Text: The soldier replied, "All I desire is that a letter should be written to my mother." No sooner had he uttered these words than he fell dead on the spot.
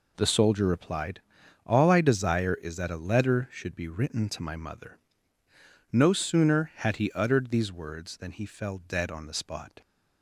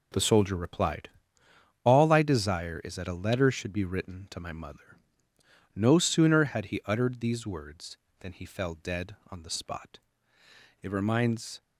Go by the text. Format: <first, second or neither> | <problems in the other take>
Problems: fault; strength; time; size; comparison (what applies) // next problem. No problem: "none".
first | goes on to say "It reminds"; noticeable; from 10.8 s on; 0.80 s long